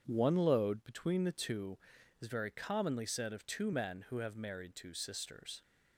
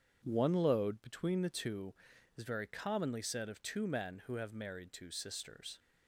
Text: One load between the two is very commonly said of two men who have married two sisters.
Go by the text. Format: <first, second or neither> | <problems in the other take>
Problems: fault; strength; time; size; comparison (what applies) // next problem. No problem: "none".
neither | starts louder than the rest; strong; the same in both